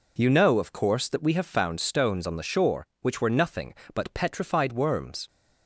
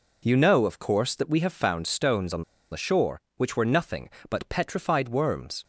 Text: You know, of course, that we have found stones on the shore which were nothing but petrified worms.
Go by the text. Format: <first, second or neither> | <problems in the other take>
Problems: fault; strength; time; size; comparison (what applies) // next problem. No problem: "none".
first | pauses between "on" and "the"; slight; at 2.4 s; 0.27 s long